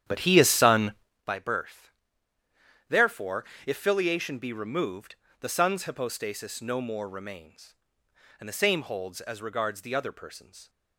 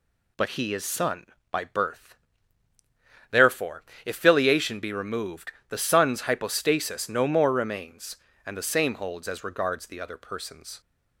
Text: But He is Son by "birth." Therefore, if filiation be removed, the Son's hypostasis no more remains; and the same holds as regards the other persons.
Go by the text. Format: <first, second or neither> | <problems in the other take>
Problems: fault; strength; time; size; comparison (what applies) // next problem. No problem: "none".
second | starts louder than the rest; strong; until 1.2 s; 10 dB